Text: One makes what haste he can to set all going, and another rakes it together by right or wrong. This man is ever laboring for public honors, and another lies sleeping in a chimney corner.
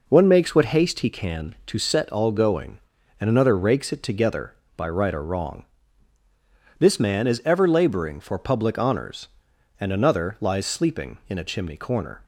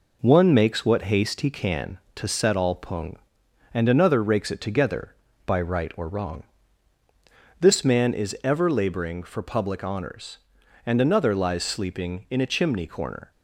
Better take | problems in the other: first | says "pung" for "going"; at 2.7 s

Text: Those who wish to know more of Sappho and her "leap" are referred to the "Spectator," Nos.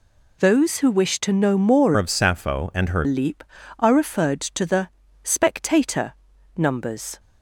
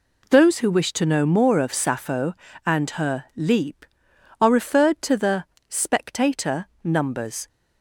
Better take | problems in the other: second | changes voice from "of" to "her"; from 1.9 to 3.0 s; 1.1 s long // pauses between "the" and "Spectator"; slight; at 4.8 s; 0.34 s long; slight in the second

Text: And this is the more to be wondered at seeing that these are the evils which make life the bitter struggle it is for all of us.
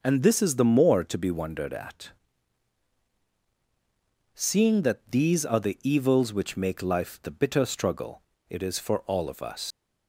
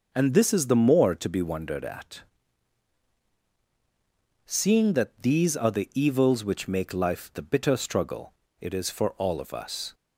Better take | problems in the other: second | pauses between "at" and "seeing"; strong; at 2.1 s; 2.2 s long; strong in the second // pauses between "struggle" and "it"; slight; at 8.2 s; 0.26 s long; slight in the second // leaves "us" unfinished; at 9.7 s; 120 ms

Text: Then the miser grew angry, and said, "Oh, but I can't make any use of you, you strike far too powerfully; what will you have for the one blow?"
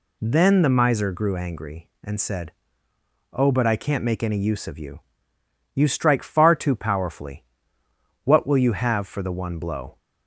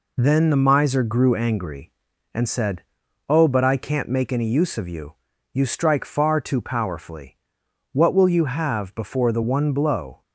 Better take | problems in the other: first | says "before" for "for"; at 8.9 s

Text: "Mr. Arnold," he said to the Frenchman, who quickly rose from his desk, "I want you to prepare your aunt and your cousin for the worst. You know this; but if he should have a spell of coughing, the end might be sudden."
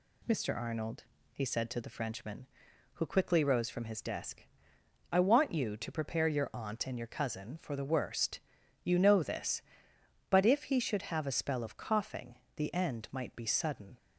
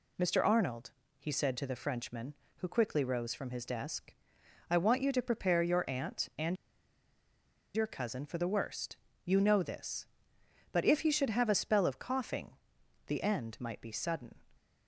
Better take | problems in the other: first | pauses between "and" and "your"; at 6.5 s; 1.1 s long

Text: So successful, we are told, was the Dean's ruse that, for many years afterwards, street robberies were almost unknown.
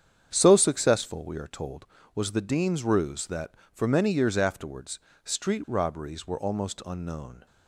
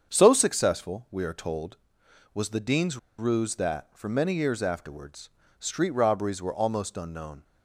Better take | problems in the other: first | starts louder than the rest; strong; until 1.1 s; 7.5 dB; strong in the first // pauses between "Dean's" and "ruse"; slight; at 2.9 s; 0.21 s long

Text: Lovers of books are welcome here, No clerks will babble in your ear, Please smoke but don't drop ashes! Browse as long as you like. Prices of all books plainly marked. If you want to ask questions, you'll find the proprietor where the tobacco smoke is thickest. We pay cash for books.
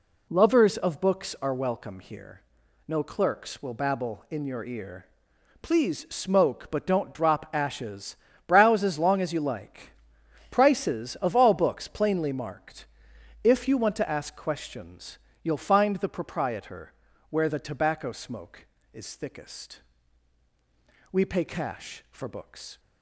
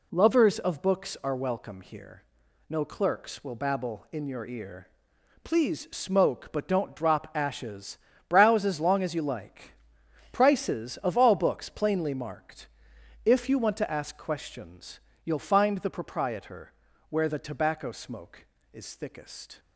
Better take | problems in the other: first | pauses between "proprietor" and "where"; at 16.7 s; 0.38 s long; also in the first // stops before "We pay cash for books"; at 19.5 s

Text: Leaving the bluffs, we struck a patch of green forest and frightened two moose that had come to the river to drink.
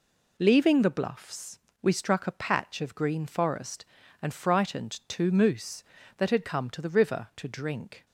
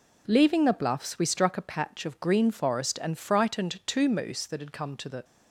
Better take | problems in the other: first | stops before "river to drink"; at 5.2 s

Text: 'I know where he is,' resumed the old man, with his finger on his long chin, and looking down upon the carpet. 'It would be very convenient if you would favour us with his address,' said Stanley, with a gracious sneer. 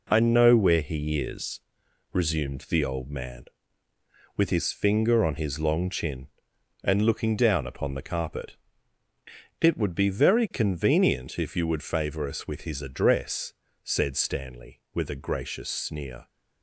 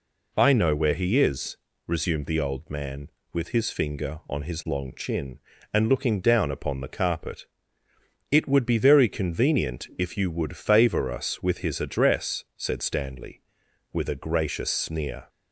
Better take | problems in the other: second | gets quieter; noticeable; throughout; 6 dB

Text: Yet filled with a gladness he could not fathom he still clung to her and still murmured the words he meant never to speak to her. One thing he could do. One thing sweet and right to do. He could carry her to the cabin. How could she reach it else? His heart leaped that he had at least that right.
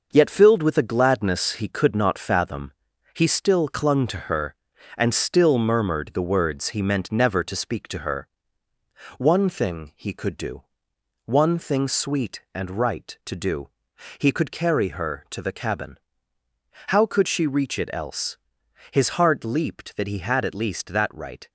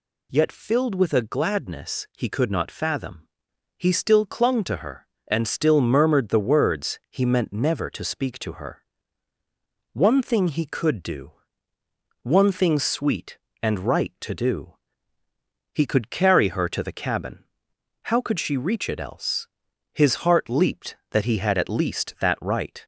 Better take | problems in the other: second | gets quieter; noticeable; throughout; 6 dB // pauses between "fathom" and "he"; at 2.7 s; 0.40 s long; noticeable in the second

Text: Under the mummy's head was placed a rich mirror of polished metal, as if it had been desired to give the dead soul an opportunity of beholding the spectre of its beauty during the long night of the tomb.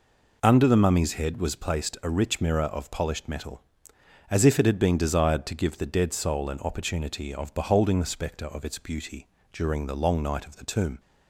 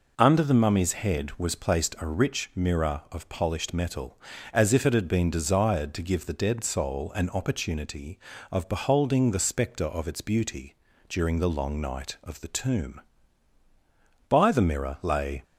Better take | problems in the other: first | pauses between "beauty" and "during"; slight; at 10.7 s; 0.34 s long; slight in the first // goes on to say "By the mirror lay"; noticeable; from 14.2 s on; 1.1 s long

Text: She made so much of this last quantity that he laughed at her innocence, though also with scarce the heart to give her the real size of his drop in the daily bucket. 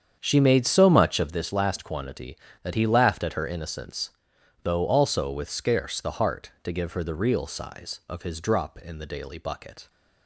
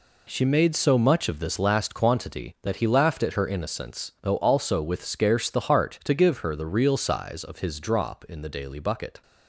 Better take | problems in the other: second | starts louder than the rest; strong; until 1.3 s; 8 dB

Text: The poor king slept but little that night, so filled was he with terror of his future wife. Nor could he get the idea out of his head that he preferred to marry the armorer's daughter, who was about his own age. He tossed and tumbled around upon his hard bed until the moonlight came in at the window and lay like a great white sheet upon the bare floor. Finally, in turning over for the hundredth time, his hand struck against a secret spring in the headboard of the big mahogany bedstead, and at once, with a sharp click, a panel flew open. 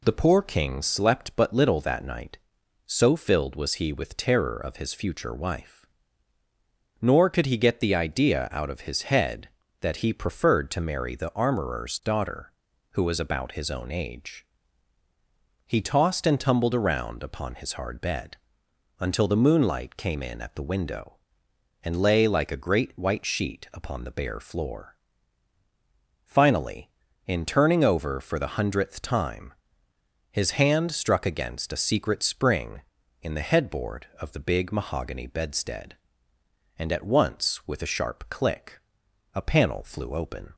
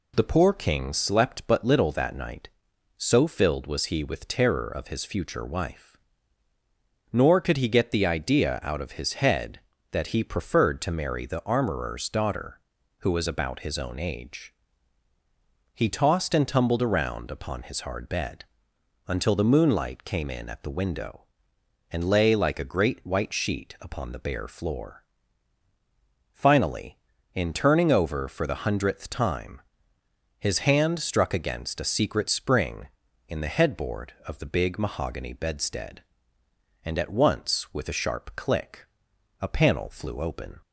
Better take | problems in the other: neither | pauses between "bed" and "until"; noticeable; the same in both

